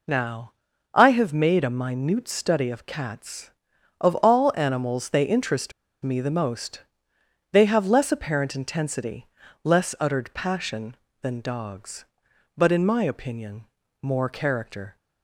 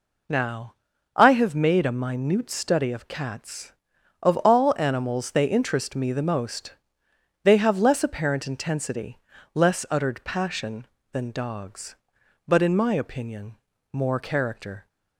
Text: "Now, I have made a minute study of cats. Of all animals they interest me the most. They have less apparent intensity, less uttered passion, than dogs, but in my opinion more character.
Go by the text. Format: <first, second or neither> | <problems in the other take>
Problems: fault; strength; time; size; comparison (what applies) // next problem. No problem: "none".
second | pauses between "interest" and "me"; slight; at 5.7 s; 0.31 s long // pauses between "opinion" and "more"; slight; at 13.6 s; 0.36 s long; slight in the second